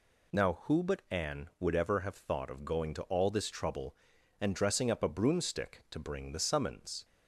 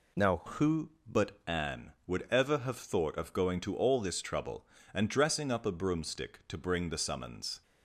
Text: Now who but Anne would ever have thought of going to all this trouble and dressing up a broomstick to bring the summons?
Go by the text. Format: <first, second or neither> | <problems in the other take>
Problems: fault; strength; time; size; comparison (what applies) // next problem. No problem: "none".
first | changes voice at "who"; from 0.4 s on; 7.2 s long